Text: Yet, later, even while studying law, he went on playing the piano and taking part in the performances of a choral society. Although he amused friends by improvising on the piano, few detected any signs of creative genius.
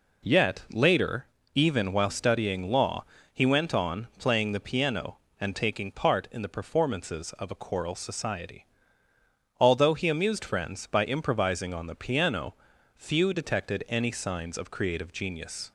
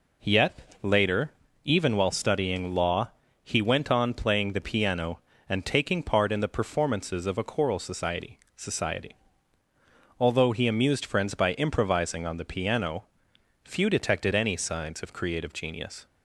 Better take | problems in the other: first | says "society" twice; at 8.5 s

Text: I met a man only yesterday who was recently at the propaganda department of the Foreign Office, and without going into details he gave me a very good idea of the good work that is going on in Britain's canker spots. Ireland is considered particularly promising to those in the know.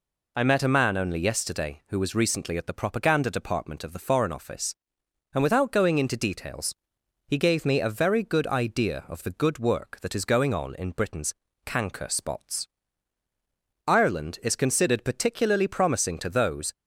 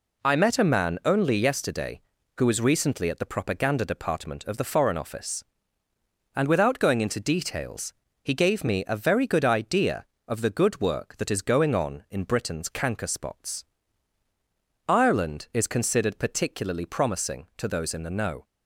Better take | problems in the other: second | pauses between "details" and "he"; noticeable; at 6.7 s; 0.54 s long; slight in the second // pauses between "Britain's" and "canker"; slight; at 11.3 s; 0.32 s long // stops before "in the know"; at 16.7 s

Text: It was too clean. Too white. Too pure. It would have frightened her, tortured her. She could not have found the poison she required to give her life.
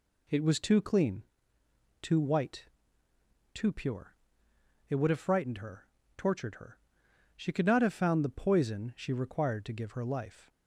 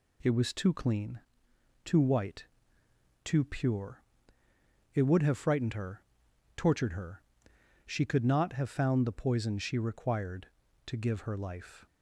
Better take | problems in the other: neither | none

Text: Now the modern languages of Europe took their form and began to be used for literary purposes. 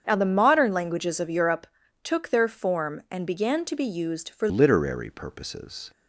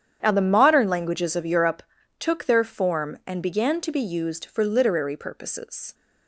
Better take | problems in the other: second | starts louder than the rest; strong; until 1.0 s; 7.5 dB; strong in the second // pauses between "Europe" and "took"; at 1.6 s; 0.38 s long; also in the second // changes voice at "literary"; from 4.4 s on; 1.5 s long

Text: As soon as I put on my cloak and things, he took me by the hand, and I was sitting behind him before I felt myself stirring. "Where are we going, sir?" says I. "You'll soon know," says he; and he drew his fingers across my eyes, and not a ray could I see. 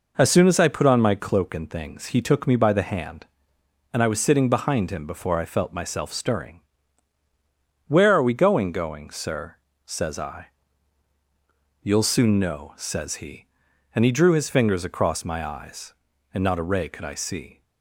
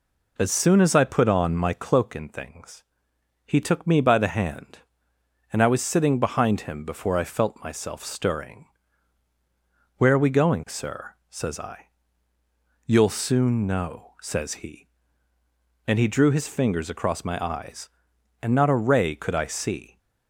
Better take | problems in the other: second | says "going" twice; at 8.7 s

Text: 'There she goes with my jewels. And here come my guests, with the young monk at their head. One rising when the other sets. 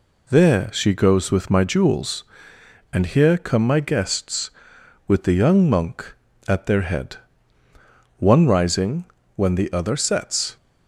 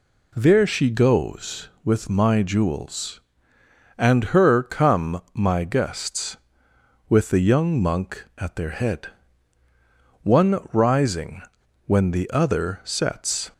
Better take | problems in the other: first | says "her" for "here"; at 4.2 s // pauses between "rising" and "when"; at 11.4 s; 0.45 s long; slight in the first

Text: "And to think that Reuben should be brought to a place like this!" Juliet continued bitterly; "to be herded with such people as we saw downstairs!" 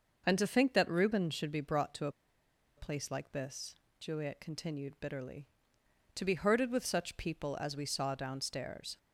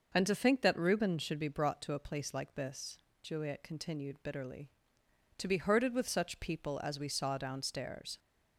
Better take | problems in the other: second | pauses between "a" and "place"; noticeable; at 2.1 s; 0.66 s long

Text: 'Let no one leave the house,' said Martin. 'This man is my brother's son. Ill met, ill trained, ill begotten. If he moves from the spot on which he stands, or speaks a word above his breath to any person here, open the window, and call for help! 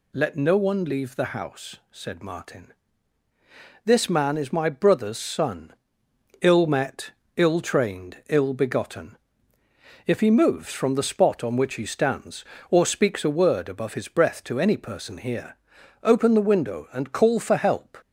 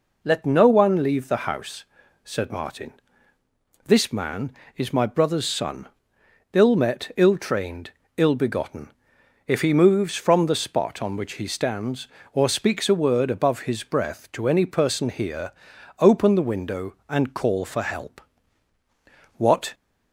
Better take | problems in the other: first | goes on to say "What"; slight; from 19.3 s on; 0.36 s long

